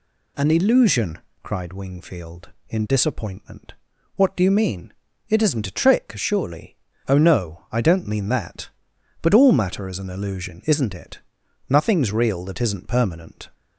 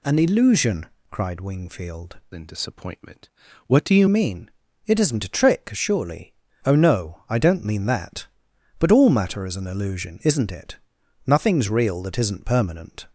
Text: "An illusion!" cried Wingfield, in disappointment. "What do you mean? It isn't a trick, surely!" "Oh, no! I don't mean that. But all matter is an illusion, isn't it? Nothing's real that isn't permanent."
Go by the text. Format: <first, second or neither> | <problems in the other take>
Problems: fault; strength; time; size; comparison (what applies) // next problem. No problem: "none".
first | changes voice from "in" to "you"; from 2.3 to 4.0 s; 1.7 s long